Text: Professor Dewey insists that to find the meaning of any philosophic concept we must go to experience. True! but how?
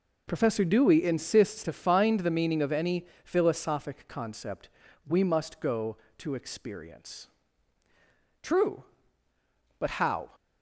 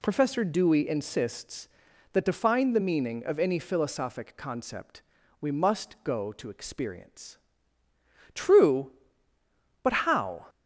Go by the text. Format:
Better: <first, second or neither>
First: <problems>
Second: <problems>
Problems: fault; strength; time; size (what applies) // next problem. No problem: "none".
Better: second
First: skips "that"; at 1.6 s // pauses between "any" and "philosophic"; slight; at 3.0 s; 0.18 s long // pauses between "concept" and "we"; at 4.6 s; 0.40 s long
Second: pauses between "concept" and "we"; at 5.0 s; 0.40 s long